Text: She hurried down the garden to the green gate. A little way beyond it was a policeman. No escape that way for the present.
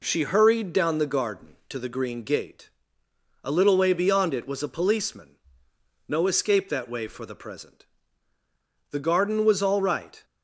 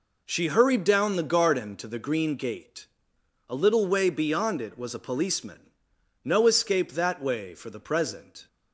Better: second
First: goes on to say "The garden was all right"; from 8.9 s on; 1.3 s long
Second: none

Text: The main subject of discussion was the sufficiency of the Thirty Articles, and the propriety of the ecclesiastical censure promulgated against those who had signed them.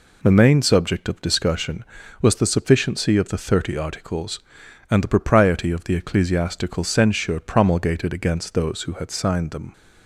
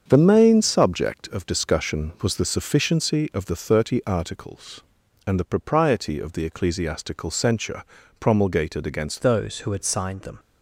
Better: first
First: none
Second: starts louder than the rest; strong; until 1.0 s; 7 dB // pauses between "censure" and "promulgated"; at 7.8 s; 0.38 s long // changes voice at "those"; from 9.2 s on; 1.1 s long

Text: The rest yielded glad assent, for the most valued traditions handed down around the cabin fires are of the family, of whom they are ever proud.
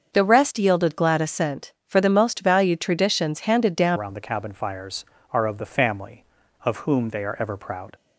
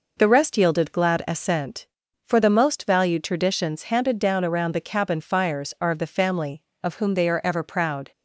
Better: second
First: starts louder than the rest; until 1.1 s; 6.5 dB // changes voice at "around"; from 3.9 s on; 4.0 s long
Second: none

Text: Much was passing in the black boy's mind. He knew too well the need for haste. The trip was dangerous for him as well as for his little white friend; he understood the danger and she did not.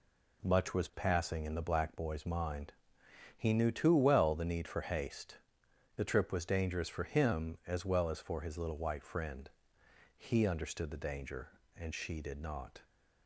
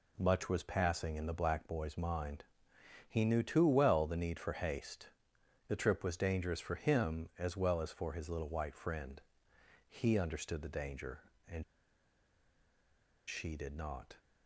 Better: first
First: none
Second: pauses between "and" and "she"; strong; at 11.6 s; 1.6 s long

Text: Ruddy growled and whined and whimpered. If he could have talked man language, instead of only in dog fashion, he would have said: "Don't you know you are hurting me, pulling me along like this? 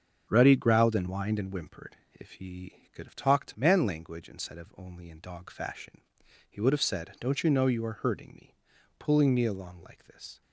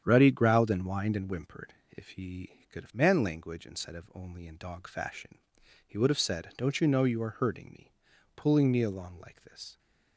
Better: first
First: starts louder than the rest; until 1.2 s; 6.5 dB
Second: starts louder than the rest; strong; until 1.0 s; 8.5 dB // skips "talked"; at 2.9 s

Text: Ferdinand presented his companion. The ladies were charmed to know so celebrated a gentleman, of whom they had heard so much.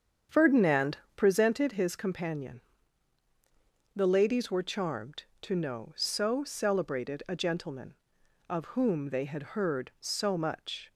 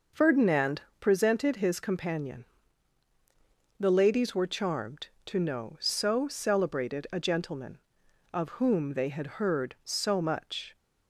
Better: second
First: starts louder than the rest; strong; until 1.7 s; 8 dB // pauses between "Ferdinand" and "presented"; slight; at 0.9 s; 0.18 s long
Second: pauses between "Ferdinand" and "presented"; slight; at 0.8 s; 0.18 s long

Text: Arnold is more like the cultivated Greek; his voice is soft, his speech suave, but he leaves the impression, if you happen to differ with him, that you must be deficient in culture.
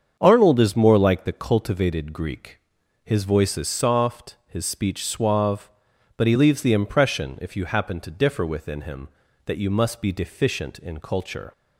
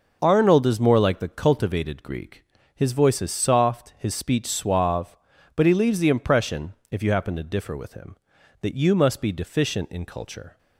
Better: second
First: starts louder than the rest; strong; until 1.2 s; 7.5 dB // says "within" for "with"; at 8.4 s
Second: none

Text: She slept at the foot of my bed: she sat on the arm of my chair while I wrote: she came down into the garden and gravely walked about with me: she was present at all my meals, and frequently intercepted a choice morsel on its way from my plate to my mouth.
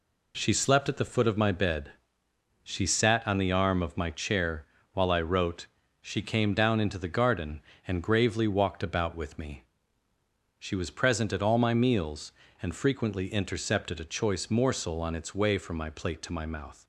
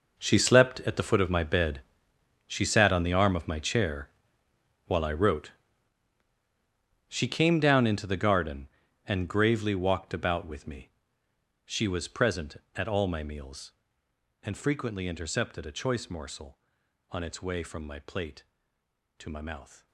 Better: first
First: pauses between "chair" and "while"; slight; at 4.6 s; 0.26 s long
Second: gets quieter; strong; throughout; 14.5 dB // pauses between "chair" and "while"; noticeable; at 4.0 s; 0.78 s long

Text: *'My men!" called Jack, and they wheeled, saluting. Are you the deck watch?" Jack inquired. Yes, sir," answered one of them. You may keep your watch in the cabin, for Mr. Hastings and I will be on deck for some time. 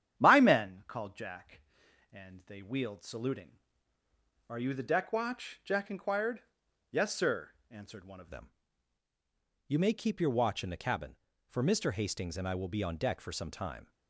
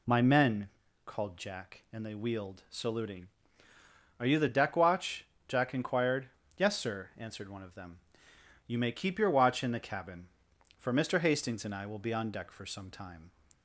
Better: second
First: starts louder than the rest; strong; until 1.2 s; 9.5 dB // changes voice at "them"; from 8.2 s on; 5.6 s long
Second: none

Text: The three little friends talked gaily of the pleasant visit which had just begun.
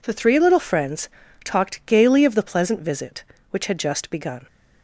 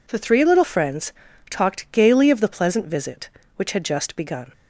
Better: neither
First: pauses between "friends" and "talked"; slight; at 1.0 s; 0.34 s long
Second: pauses between "friends" and "talked"; slight; at 1.1 s; 0.36 s long

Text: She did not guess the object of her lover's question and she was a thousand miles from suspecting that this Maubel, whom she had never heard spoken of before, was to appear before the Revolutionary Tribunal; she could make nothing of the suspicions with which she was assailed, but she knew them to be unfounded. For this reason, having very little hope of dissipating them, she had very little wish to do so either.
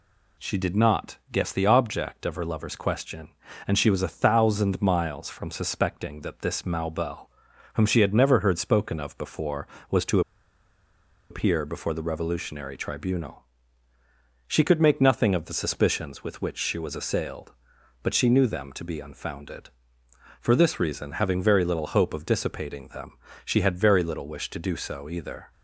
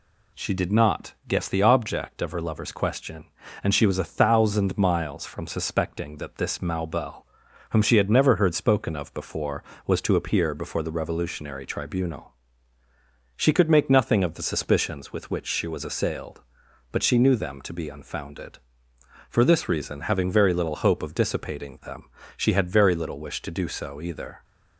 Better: second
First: pauses between "to" and "appear"; at 10.2 s; 1.0 s long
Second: none

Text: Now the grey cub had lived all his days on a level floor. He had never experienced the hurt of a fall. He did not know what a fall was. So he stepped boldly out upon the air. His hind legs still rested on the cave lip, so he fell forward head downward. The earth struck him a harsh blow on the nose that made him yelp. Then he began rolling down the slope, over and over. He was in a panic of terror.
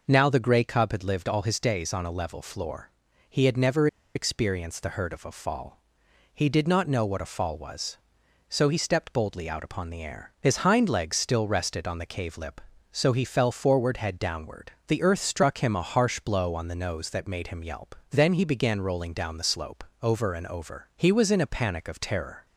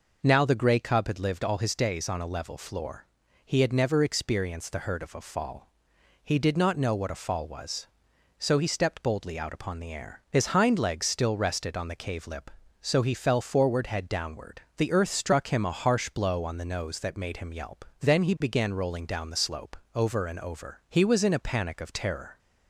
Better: second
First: pauses between "never" and "experienced"; slight; at 3.8 s; 0.28 s long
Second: none

